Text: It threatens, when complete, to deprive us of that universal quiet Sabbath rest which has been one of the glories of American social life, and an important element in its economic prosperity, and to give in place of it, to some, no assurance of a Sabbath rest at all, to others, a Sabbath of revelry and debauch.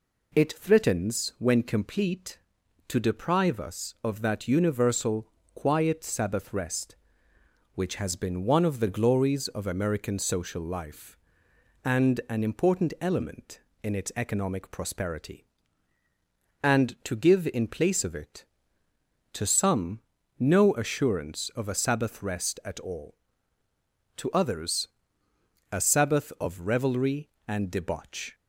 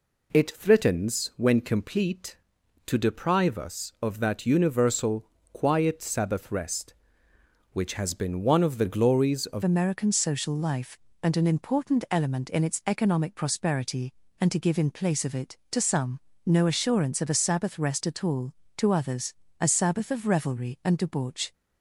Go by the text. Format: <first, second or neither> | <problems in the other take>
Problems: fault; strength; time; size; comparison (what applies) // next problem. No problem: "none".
first | pauses between "universal" and "quiet"; slight; at 5.2 s; 0.26 s long; slight in the first // changes voice at "American"; from 9.6 s on; 11.9 s long